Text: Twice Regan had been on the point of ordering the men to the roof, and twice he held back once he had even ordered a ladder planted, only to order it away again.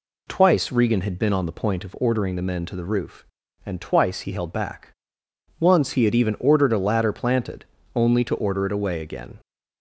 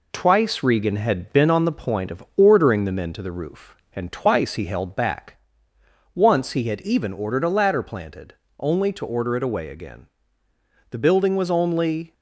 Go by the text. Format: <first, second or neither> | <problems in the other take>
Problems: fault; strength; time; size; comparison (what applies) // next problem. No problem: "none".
first | pauses between "back" and "once"; noticeable; at 5.3 s; 0.76 s long; noticeable in the first // goes on to say "The building was only"; noticeable; from 10.9 s on; 1.2 s long